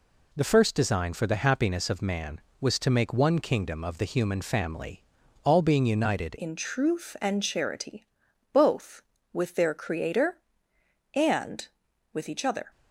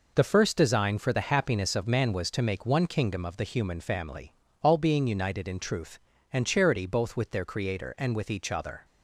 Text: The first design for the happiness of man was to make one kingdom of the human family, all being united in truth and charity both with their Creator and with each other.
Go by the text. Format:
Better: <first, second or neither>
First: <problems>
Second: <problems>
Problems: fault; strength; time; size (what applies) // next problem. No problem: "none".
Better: second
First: changes voice at "in"; from 6.3 s on; 6.4 s long // pauses between "charity" and "both"; noticeable; at 8.0 s; 0.46 s long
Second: none